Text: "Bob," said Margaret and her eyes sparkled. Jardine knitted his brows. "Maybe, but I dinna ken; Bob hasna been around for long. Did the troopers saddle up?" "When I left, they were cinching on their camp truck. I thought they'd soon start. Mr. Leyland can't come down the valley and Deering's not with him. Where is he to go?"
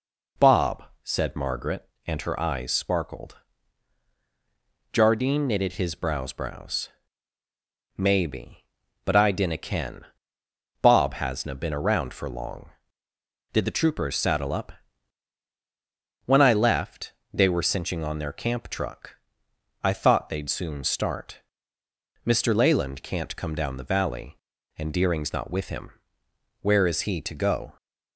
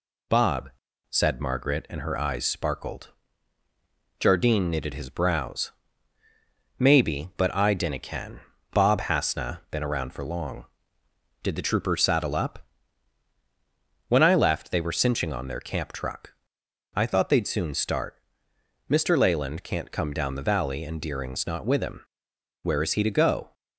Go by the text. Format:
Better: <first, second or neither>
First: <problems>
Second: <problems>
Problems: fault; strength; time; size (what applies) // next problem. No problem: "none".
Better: second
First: says "brows" twice; at 6.3 s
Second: none